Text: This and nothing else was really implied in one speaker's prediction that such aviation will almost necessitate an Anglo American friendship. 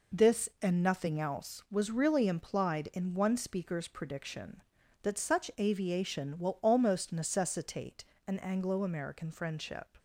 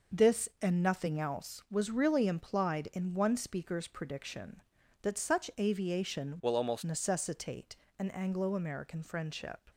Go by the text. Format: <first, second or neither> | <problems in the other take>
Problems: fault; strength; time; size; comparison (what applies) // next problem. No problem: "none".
first | changes voice from "will" to "almost"; from 6.4 to 6.8 s; 0.4 s long // pauses between "necessitate" and "an"; slight; at 7.7 s; 0.24 s long; slight in the first